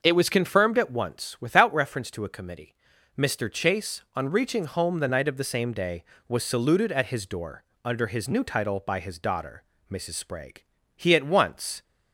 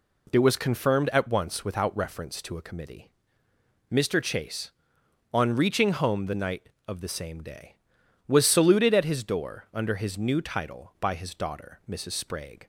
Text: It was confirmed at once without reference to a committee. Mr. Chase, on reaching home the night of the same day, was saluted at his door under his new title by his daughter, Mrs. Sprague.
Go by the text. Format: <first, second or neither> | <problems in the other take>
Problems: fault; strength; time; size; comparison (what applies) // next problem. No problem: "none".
second | starts louder than the rest; until 1.0 s; 6 dB // pauses between "door" and "under"; slight; at 7.6 s; 0.20 s long // goes on to say "He at once"; noticeable; from 10.9 s on; 0.88 s long